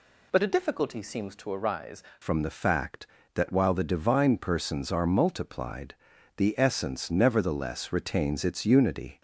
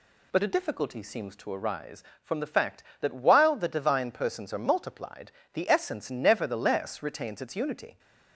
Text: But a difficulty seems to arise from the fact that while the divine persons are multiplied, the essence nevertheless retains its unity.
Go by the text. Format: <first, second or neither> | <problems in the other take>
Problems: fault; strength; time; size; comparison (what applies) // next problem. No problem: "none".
second | changes voice at "from"; from 2.2 s on; 7.0 s long